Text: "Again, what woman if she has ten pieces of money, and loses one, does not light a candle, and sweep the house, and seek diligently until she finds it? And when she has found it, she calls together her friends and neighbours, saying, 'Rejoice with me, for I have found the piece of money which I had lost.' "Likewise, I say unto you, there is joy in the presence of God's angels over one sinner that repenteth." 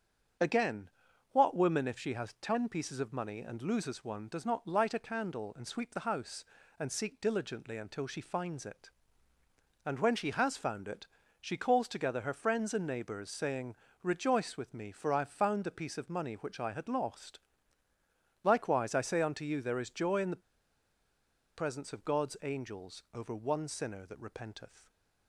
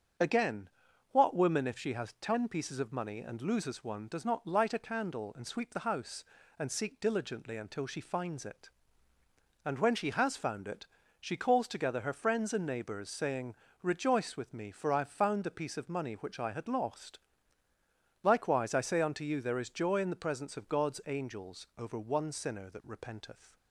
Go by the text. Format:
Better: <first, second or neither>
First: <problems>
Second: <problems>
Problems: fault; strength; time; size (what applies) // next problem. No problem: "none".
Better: second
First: starts louder than the rest; strong; until 1.8 s; 7.5 dB // pauses between "the" and "presence"; at 20.4 s; 1.1 s long // stays silent after the last word; slight; from 24.7 s on; 0.5 s long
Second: starts louder than the rest; strong; until 1.6 s; 7.5 dB